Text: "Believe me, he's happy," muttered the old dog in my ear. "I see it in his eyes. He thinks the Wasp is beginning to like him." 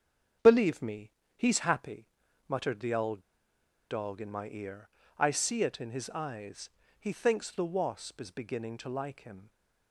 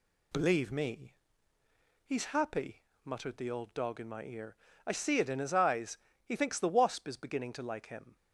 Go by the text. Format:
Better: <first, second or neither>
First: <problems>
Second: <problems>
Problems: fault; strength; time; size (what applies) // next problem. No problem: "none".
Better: second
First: starts louder than the rest; strong; until 1.6 s; 7.5 dB // pauses between "old" and "dog"; noticeable; at 3.2 s; 0.68 s long // stays silent after the last word; slight; from 9.4 s on; 0.5 s long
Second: none